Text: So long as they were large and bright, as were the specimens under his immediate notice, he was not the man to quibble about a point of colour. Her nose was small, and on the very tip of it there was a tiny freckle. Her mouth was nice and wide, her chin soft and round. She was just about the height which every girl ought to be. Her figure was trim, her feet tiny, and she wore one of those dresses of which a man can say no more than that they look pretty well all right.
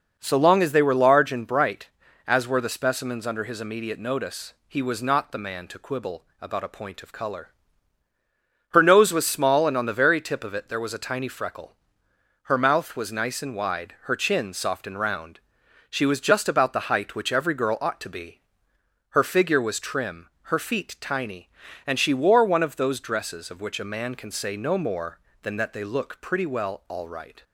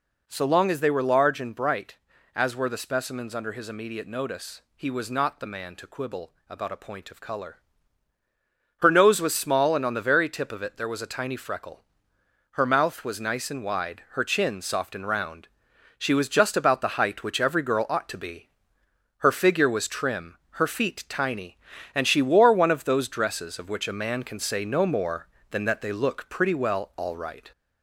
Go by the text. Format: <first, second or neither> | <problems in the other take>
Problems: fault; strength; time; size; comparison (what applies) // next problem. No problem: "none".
first | gets louder; slight; throughout; 2.5 dB // pauses between "quibble" and "about"; slight; at 6.3 s; 0.18 s long; slight in the first